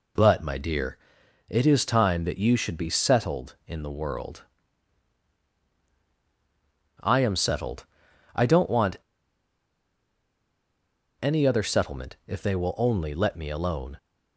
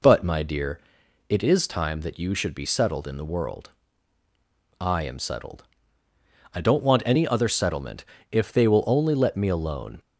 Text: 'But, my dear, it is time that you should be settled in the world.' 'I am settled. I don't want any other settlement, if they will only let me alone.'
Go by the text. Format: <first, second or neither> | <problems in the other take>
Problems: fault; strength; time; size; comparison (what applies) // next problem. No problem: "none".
second | pauses between "want" and "any"; strong; at 8.9 s; 2.2 s long